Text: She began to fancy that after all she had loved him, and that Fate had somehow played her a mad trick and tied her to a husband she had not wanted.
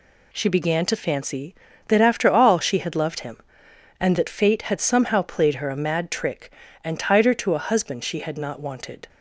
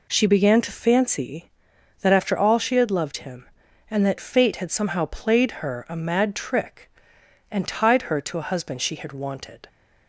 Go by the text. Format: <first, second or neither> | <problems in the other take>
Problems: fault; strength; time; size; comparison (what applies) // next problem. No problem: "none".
first | skips "not"; at 9.1 s